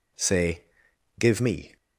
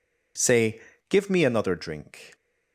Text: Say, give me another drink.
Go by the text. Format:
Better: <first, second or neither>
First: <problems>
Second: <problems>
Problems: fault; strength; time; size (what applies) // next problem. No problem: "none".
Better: second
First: stops before "another drink"; at 1.7 s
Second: none